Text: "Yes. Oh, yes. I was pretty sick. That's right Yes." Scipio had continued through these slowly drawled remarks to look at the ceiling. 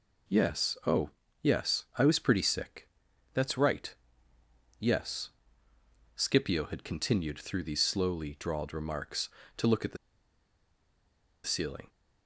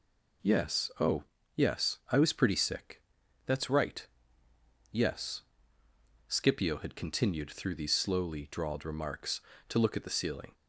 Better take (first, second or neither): second